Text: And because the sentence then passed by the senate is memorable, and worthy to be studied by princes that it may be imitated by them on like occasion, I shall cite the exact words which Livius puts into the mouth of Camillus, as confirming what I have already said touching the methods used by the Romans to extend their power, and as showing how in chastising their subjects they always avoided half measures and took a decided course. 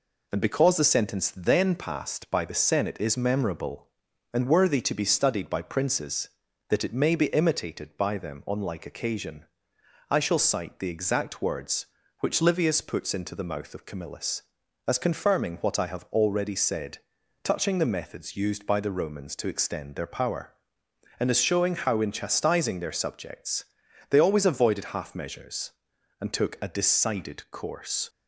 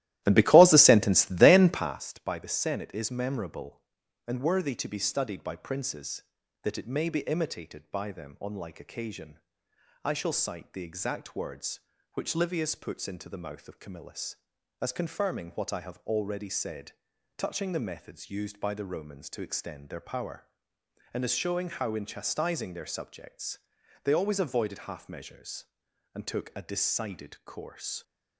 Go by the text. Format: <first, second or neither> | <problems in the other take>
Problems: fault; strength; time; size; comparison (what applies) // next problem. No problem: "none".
first | starts louder than the rest; strong; until 2.0 s; 15 dB // pauses between "said" and "touching"; noticeable; at 16.9 s; 0.46 s long; noticeable in the first // pauses between "subjects" and "they"; noticeable; at 23.5 s; 0.46 s long; noticeable in the first